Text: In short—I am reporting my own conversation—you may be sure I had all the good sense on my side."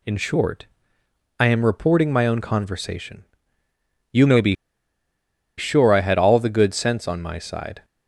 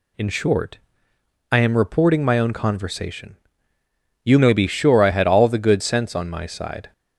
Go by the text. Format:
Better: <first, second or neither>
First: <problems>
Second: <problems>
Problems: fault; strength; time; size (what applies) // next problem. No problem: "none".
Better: second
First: pauses between "be" and "sure"; at 4.5 s; 1.0 s long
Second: none